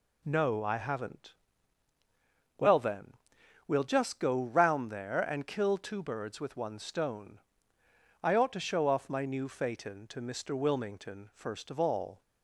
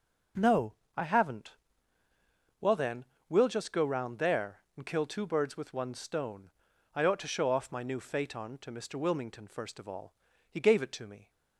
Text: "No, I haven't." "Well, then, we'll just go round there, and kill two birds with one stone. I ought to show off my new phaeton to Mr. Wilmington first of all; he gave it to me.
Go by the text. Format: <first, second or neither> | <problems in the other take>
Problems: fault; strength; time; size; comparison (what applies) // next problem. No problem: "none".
second | stops before "he gave it to me"; at 12.2 s